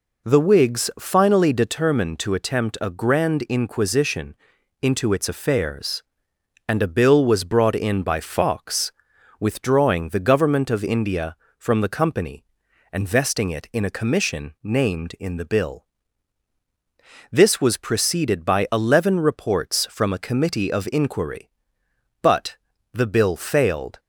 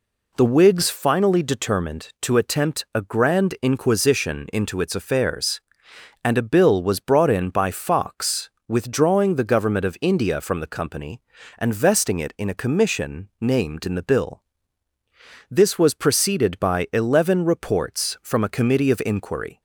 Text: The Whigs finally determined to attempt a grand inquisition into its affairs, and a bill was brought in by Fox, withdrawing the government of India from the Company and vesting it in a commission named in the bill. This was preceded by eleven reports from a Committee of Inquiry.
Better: second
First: pauses between "inquisition" and "into"; noticeable; at 4.3 s; 0.46 s long // goes on to say "But the bill failed"; strong; from 22.2 s on; 1.7 s long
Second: none

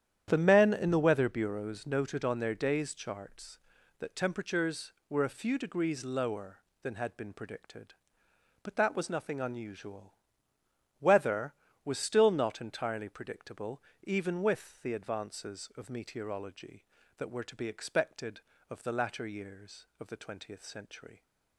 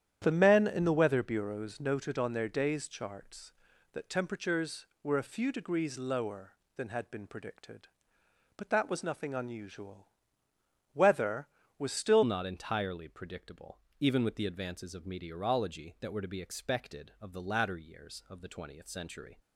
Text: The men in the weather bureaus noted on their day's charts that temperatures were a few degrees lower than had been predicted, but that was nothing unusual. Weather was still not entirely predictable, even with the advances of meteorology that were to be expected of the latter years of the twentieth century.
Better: first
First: starts louder than the rest; strong; until 1.2 s; 10 dB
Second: starts louder than the rest; strong; until 1.2 s; 10 dB // changes voice at "not"; from 12.2 s on; 7.1 s long

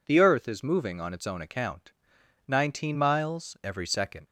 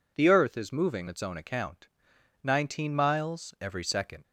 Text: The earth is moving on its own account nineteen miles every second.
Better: first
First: pauses between "account" and "nineteen"; noticeable; at 1.9 s; 0.52 s long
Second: skips "on"; at 1.0 s // pauses between "account" and "nineteen"; noticeable; at 1.8 s; 0.52 s long

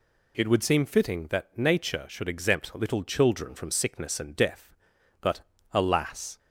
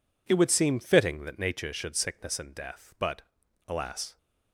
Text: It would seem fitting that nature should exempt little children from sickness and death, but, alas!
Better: first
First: none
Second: skips "exempt little children from"; at 1.9 s

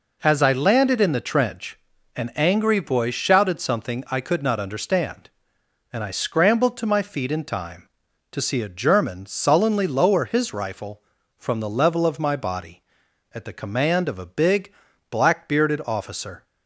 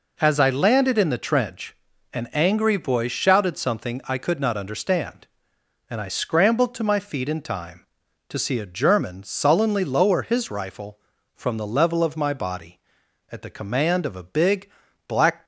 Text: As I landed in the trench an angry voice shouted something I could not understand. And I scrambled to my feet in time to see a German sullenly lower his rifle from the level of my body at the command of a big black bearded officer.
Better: first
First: pauses between "trench" and "an"; at 1.7 s; 0.38 s long // pauses between "big" and "black"; slight; at 14.7 s; 0.36 s long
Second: pauses between "trench" and "an"; at 1.7 s; 0.38 s long // pauses between "big" and "black"; slight; at 14.7 s; 0.36 s long // stops before "bearded officer"; at 15.4 s

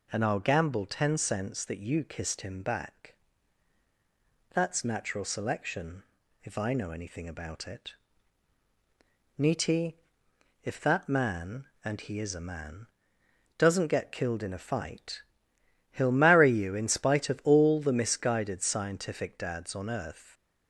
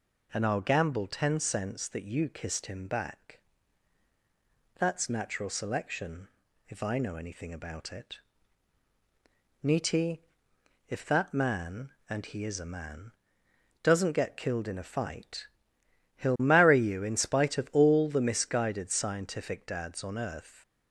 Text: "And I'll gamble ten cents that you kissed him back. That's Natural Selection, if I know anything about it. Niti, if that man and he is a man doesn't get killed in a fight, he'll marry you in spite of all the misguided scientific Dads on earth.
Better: neither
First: pauses between "man" and "doesn't"; noticeable; at 12.8 s; 0.72 s long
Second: pauses between "man" and "doesn't"; noticeable; at 13.1 s; 0.72 s long

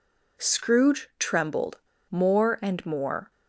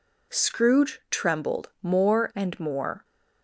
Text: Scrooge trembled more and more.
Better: second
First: pauses between "trembled" and "more"; slight; at 1.7 s; 0.32 s long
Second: none

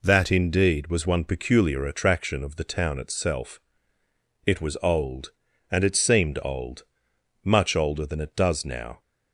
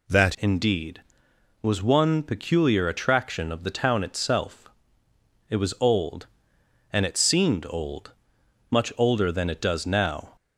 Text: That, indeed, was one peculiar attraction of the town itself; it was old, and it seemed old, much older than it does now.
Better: first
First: none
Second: changes voice at "indeed"; from 0.3 s on; 10.0 s long

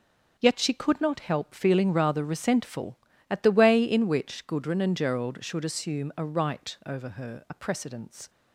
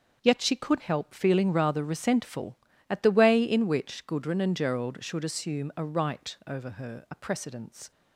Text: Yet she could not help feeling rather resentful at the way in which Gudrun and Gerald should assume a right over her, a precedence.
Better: first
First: starts louder than the rest; noticeable; until 1.3 s; 6 dB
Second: starts louder than the rest; until 1.2 s; 6 dB // skips "not"; at 0.8 s

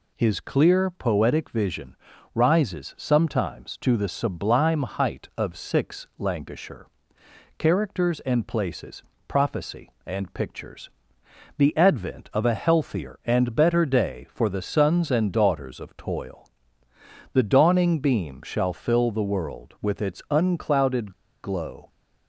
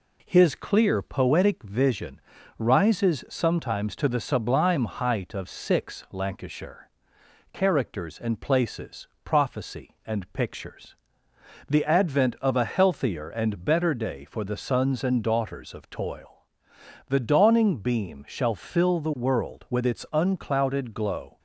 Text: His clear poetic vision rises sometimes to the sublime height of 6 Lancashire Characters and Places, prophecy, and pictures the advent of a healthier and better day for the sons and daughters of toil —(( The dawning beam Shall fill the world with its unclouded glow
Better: second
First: pauses between "vision" and "rises"; at 1.9 s; 0.38 s long // pauses between "Lancashire" and "Characters"; noticeable; at 6.8 s; 0.72 s long // pauses between "pictures" and "the"; noticeable; at 10.8 s; 0.68 s long // pauses between "unclouded" and "glow"; slight; at 21.1 s; 0.32 s long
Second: pauses between "vision" and "rises"; slight; at 2.2 s; 0.36 s long // pauses between "Lancashire" and "Characters"; noticeable; at 6.8 s; 0.64 s long // pauses between "pictures" and "the"; noticeable; at 10.9 s; 0.72 s long

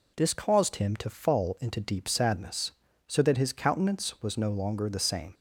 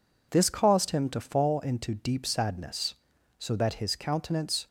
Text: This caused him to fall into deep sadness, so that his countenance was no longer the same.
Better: first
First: none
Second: stops before "was no longer the same"; at 4.6 s

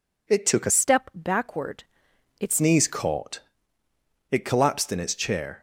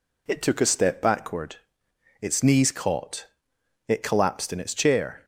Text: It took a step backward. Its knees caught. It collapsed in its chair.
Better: second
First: changes voice from "step" to "Its"; from 0.6 to 2.6 s; 2.0 s long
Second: none

